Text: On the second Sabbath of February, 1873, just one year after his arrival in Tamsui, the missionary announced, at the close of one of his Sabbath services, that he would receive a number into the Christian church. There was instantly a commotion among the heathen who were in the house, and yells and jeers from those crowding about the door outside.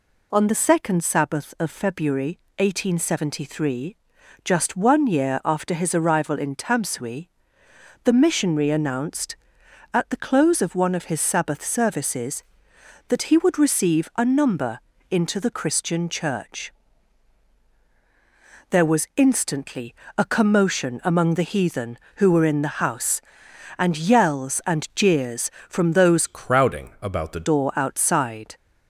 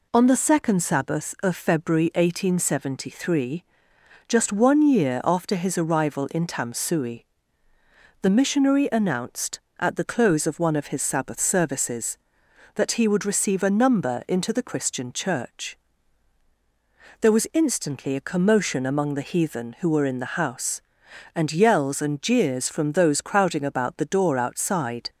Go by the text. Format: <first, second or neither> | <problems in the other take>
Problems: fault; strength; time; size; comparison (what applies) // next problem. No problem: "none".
second | pauses between "number" and "into"; slight; at 14.7 s; 0.30 s long // pauses between "instantly" and "a"; slight; at 19.9 s; 0.24 s long // changes voice from "crowding" to "the"; from 26.2 to 27.4 s; 1.2 s long